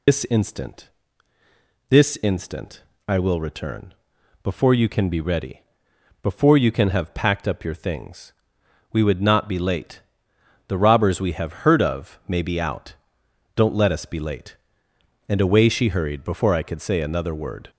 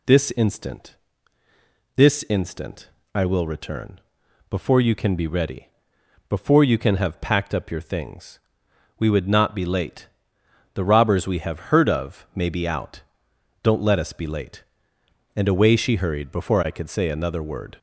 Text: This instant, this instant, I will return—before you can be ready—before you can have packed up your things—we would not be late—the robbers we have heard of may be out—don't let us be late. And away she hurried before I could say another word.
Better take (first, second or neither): second